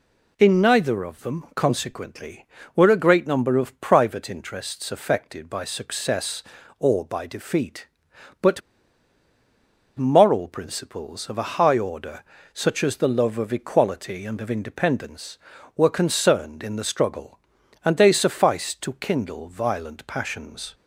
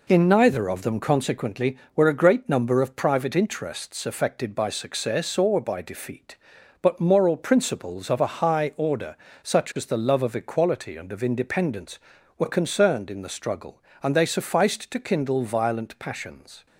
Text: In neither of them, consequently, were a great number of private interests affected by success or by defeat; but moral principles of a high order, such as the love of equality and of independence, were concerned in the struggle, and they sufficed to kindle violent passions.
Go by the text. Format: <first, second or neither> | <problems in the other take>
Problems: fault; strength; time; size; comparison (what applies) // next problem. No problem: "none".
second | pauses between "but" and "moral"; strong; at 8.6 s; 1.3 s long